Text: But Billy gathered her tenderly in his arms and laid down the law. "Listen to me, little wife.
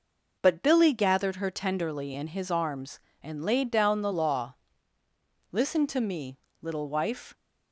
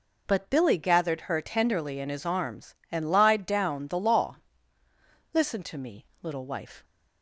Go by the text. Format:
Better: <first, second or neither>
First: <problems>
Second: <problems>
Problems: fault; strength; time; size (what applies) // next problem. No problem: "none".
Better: first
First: none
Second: says "lied" for "laid"; at 3.1 s